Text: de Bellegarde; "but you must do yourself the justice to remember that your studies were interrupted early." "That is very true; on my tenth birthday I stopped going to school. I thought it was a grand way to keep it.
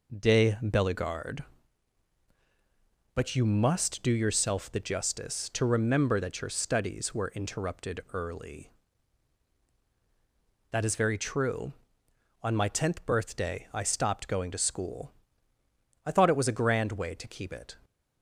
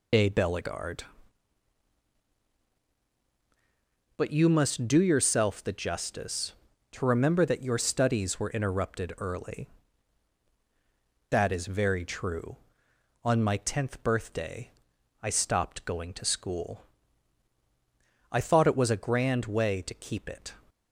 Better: first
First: none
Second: loses the start of "de"; at 0.1 s; 65 ms // pauses between "birthday" and "I"; noticeable; at 14.6 s; 0.54 s long

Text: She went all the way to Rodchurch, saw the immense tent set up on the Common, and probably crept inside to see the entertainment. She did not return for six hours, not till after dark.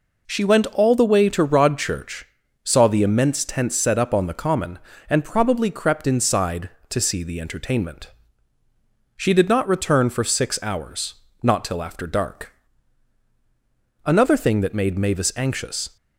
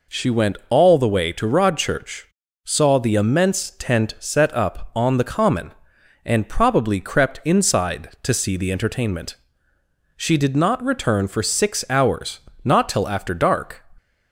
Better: second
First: goes on to say "Another thing that made Mavis anxious"; strong; from 14.0 s on; 1.9 s long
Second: none

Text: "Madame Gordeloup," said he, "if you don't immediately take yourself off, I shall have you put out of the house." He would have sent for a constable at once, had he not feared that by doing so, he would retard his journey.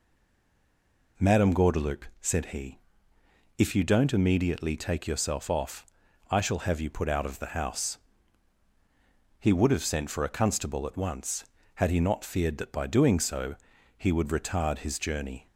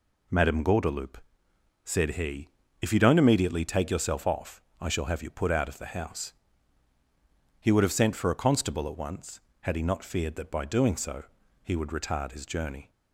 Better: second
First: stays silent before the first word; until 1.1 s; 1.1 s long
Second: none

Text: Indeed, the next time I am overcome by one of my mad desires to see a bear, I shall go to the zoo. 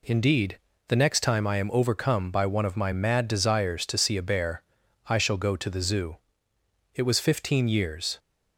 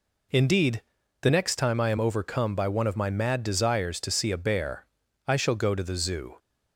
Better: second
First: goes on to say "It was fifteen years"; noticeable; from 6.9 s on; 1.2 s long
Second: none

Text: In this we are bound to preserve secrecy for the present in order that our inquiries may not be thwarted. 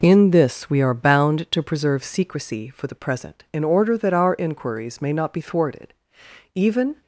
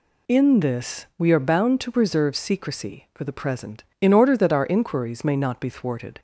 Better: second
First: goes on to say "Even"; slight; from 6.5 s on; 0.46 s long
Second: none

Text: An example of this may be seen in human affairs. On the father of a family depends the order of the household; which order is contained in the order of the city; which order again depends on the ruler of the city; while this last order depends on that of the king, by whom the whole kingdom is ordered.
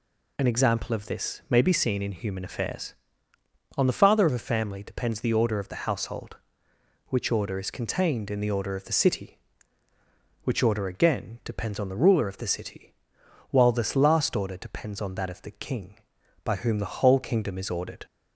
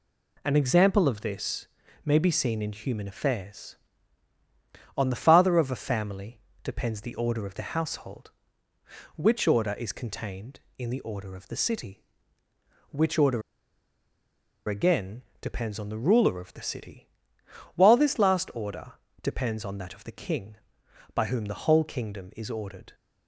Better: first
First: none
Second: pauses between "this" and "may"; slight; at 1.6 s; 0.36 s long // pauses between "family" and "depends"; slight; at 6.3 s; 0.24 s long // pauses between "order" and "again"; strong; at 13.4 s; 1.2 s long // pauses between "again" and "depends"; slight; at 15.2 s; 0.18 s long // pauses between "order" and "depends"; slight; at 18.9 s; 0.28 s long

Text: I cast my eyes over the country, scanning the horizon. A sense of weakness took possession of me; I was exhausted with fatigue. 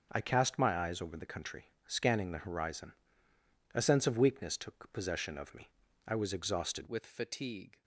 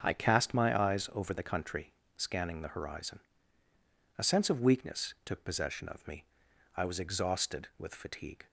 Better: second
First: starts louder than the rest; until 1.1 s; 6 dB // changes voice at "with"; from 6.8 s on; 1.0 s long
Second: starts louder than the rest; strong; until 1.0 s; 7 dB

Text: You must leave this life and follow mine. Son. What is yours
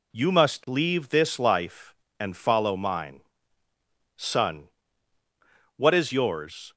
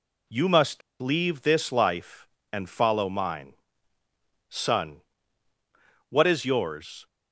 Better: first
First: none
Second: pauses between "must" and "leave"; slight; at 0.8 s; 0.20 s long

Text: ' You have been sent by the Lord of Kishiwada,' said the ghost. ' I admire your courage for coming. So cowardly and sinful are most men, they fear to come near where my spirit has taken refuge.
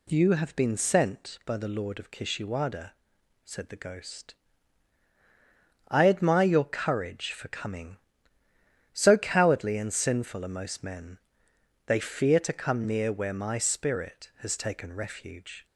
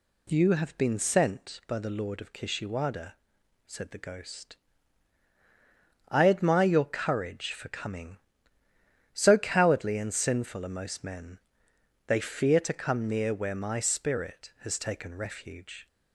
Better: neither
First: none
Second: none

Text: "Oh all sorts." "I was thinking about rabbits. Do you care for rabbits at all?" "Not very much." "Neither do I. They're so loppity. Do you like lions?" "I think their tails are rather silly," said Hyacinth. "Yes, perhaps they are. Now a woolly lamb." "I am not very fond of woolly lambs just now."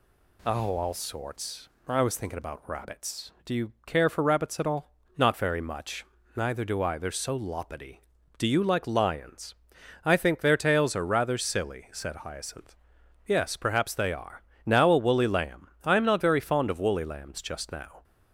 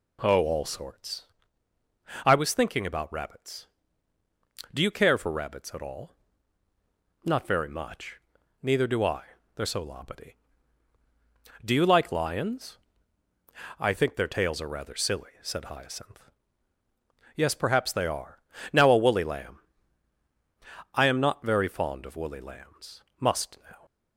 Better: first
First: none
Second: says "must" for "just"; at 23.1 s

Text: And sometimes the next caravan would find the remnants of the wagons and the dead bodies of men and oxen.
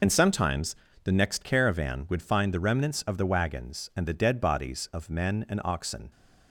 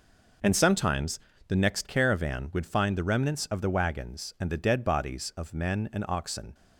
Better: second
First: loses the start of "And"; at 0.0 s; 40 ms // pauses between "sometimes" and "the"; slight; at 0.7 s; 0.28 s long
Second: pauses between "sometimes" and "the"; slight; at 1.1 s; 0.28 s long

